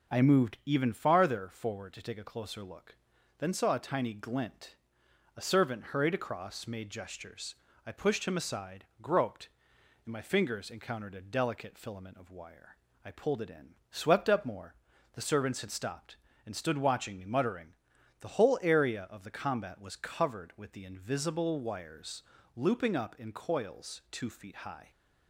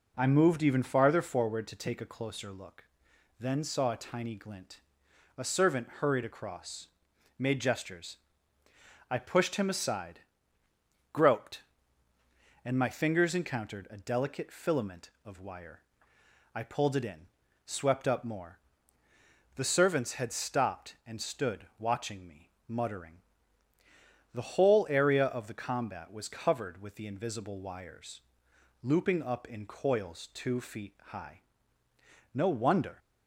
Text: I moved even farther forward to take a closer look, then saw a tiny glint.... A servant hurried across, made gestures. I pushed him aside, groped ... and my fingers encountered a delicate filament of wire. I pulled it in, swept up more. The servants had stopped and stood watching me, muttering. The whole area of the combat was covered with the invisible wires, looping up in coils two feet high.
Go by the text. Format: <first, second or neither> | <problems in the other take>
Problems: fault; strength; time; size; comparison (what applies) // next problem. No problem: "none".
first | pauses between "stood" and "watching"; slight; at 21.6 s; 0.16 s long // goes on to say "No wonder"; noticeable; from 32.3 s on; 0.66 s long